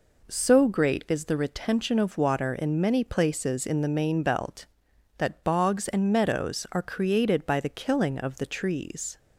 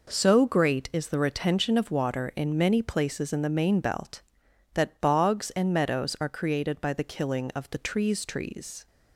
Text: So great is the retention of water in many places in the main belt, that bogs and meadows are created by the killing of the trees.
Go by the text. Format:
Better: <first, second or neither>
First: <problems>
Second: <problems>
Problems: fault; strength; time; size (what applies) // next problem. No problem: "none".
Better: first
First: none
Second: says "trees" twice; at 8.2 s